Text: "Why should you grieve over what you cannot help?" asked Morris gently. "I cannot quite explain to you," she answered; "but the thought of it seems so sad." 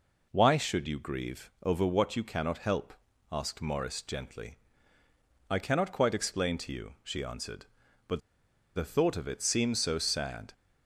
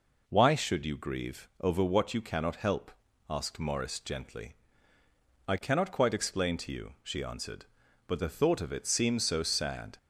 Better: second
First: pauses between "but" and "the"; noticeable; at 8.1 s; 0.57 s long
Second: none

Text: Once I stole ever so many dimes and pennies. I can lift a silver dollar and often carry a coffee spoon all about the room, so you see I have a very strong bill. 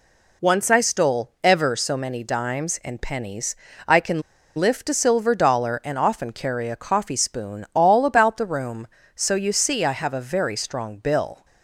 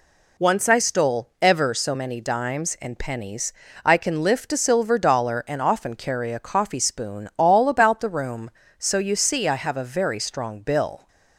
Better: second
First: pauses between "can" and "lift"; at 4.2 s; 0.36 s long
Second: none

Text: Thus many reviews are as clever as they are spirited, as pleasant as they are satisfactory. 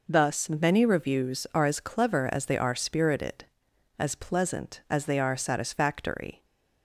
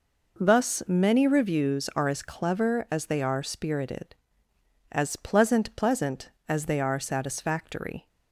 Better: first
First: none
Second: says "pleasant" twice; at 5.7 s

